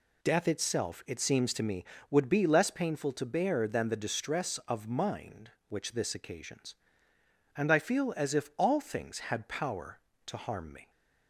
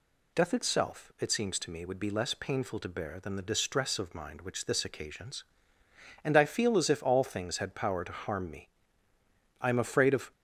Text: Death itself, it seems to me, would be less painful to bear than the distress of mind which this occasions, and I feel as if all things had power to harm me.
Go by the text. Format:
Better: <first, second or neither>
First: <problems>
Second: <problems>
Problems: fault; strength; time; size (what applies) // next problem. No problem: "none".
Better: first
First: none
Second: goes on to say "I am afraid of"; noticeable; from 9.5 s on; 0.72 s long